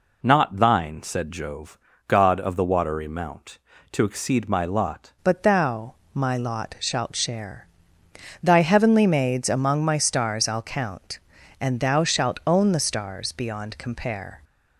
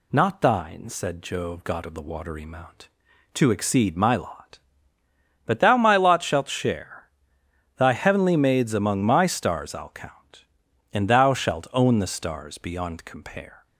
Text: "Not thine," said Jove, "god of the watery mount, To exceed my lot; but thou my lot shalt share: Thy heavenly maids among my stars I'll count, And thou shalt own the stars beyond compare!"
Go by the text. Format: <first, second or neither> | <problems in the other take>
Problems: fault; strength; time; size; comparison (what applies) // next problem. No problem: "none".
second | changes voice at "but"; from 5.2 s on; 9.2 s long // pauses between "thou" and "my"; slight; at 5.9 s; 0.18 s long